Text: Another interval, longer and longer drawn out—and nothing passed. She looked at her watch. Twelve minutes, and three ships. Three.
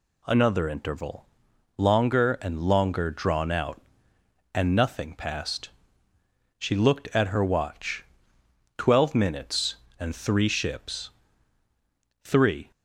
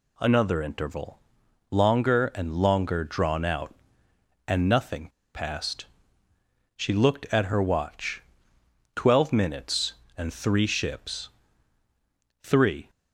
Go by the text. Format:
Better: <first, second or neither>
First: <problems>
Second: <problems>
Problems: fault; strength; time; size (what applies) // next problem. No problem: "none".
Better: first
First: none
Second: pauses between "nothing" and "passed"; slight; at 5.0 s; 0.25 s long